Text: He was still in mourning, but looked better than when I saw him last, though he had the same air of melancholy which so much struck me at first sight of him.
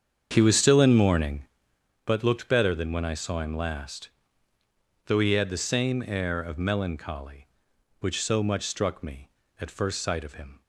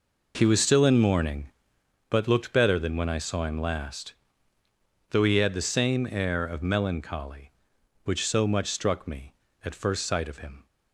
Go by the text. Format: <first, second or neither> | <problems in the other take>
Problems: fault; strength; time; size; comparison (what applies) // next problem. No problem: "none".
second | starts louder than the rest; strong; until 1.5 s; 7.5 dB